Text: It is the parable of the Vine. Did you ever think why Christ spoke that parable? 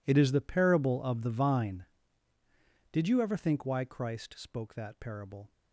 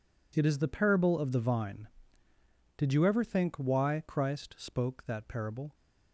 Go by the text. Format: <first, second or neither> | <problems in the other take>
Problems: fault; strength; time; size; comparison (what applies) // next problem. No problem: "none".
second | gets quieter; strong; throughout; 17.5 dB